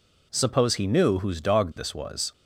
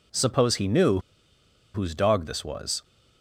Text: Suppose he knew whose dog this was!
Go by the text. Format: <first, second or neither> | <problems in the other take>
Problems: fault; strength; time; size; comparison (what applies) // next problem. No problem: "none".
first | pauses between "knew" and "whose"; noticeable; at 0.9 s; 0.74 s long